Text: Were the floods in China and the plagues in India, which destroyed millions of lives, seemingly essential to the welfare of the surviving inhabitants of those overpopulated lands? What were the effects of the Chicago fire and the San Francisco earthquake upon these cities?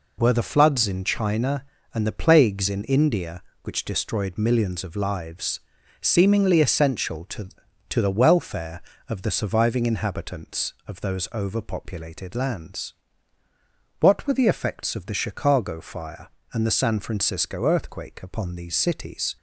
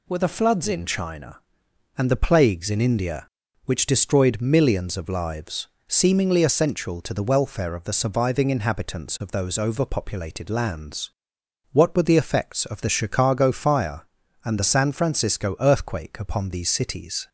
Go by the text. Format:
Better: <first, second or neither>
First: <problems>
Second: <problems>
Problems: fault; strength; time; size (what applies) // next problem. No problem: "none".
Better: second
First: says "to" twice; at 7.9 s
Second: none